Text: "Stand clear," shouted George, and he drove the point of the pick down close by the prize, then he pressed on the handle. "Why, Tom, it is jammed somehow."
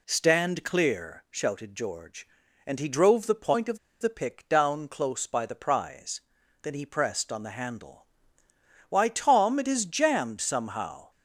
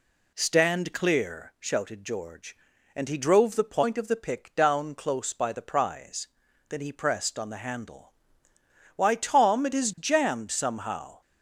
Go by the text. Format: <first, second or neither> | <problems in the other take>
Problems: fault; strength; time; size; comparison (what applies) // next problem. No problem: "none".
second | pauses between "of" and "the"; slight; at 3.7 s; 0.22 s long